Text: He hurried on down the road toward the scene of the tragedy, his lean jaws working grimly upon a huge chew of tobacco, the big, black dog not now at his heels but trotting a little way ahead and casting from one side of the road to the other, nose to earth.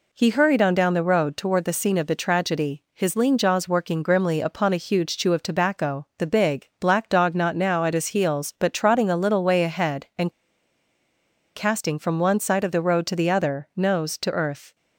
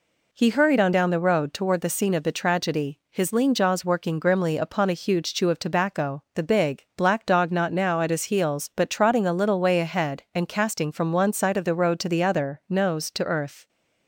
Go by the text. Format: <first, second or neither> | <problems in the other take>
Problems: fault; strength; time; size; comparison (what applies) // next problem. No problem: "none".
second | pauses between "and" and "casting"; at 10.3 s; 1.2 s long